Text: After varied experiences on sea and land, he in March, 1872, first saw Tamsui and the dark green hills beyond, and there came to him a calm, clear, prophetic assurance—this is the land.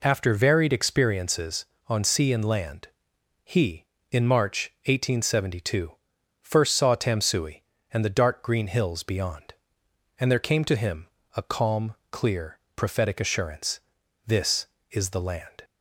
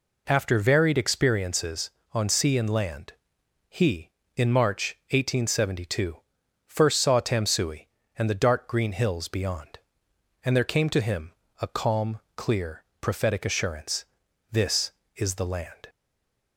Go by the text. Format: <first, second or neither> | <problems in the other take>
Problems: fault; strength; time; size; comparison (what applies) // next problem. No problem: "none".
first | pauses between "him" and "a"; slight; at 11.3 s; 0.28 s long; slight in the first // stays silent after the last word; slight; from 15.8 s on; 0.7 s long